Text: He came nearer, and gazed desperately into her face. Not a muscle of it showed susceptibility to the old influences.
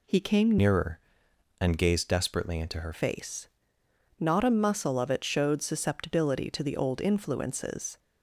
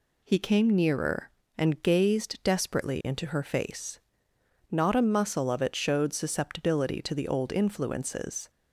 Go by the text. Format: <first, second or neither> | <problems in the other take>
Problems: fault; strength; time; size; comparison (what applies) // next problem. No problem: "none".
second | changes voice from "nearer" to "her"; from 0.5 to 2.9 s; 2.4 s long